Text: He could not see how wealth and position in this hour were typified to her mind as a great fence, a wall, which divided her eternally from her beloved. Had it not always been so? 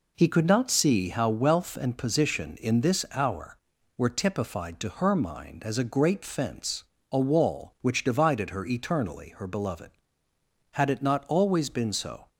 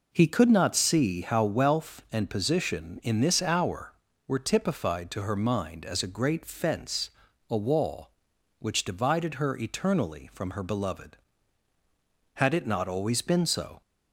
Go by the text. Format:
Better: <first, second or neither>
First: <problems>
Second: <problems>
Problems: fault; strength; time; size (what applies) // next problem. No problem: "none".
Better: second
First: skips "from"; at 9.3 s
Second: none